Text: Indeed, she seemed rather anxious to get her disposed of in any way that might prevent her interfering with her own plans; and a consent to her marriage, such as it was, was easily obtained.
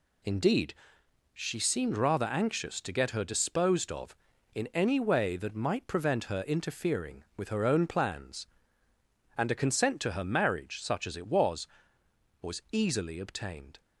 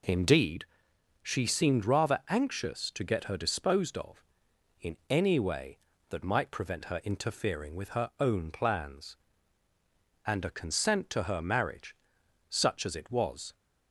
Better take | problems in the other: first | stops before "was easily obtained"; at 13.5 s

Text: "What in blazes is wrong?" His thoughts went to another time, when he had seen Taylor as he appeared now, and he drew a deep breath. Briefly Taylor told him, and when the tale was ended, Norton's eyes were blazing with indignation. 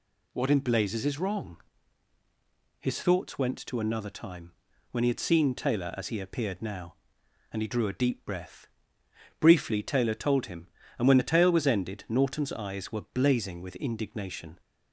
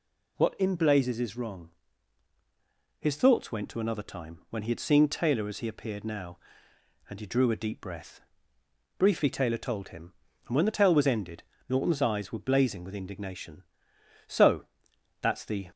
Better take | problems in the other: first | goes on to say "So that's the"; from 14.2 s on; 1.4 s long

